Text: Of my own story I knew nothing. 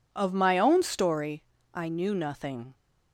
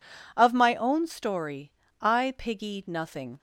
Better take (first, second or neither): first